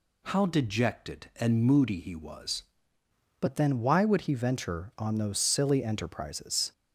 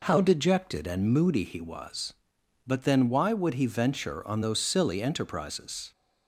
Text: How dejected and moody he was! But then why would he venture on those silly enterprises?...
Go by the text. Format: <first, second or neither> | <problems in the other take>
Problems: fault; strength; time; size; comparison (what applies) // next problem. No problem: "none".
second | changes voice at "But"; from 3.3 s on; 3.4 s long